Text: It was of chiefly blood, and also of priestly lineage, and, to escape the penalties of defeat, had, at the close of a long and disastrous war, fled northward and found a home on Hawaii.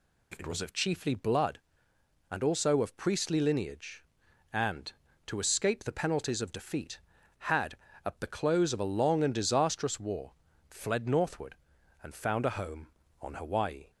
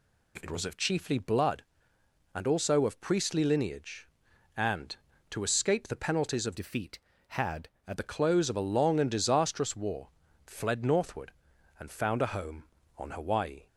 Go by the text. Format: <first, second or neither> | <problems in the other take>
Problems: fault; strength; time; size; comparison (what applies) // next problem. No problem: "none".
first | changes voice from "defeat" to "at"; from 6.5 to 7.9 s; 1.4 s long